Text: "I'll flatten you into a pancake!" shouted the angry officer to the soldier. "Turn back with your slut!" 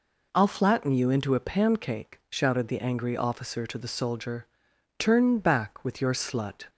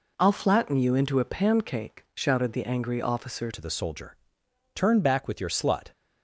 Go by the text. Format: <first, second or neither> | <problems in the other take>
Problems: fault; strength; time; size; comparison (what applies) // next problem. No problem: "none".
first | changes voice at "to"; from 3.5 s on; 2.3 s long